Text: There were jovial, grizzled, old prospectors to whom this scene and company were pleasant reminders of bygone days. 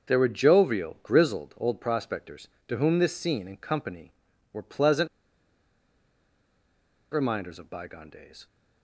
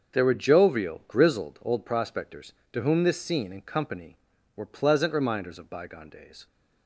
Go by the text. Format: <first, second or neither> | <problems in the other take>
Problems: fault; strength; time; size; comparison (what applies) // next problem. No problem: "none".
second | starts louder than the rest; until 1.1 s; 6.5 dB; also in the second // pauses between "pleasant" and "reminders"; strong; at 5.0 s; 2.0 s long